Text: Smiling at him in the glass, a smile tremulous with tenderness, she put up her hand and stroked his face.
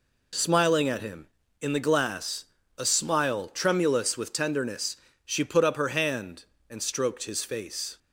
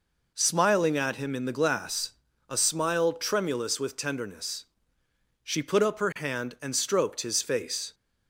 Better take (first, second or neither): neither